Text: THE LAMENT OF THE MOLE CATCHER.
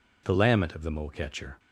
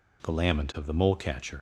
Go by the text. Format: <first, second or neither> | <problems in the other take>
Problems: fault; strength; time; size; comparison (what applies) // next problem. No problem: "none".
first | leaves "CATCHER" unfinished; at 1.5 s; 75 ms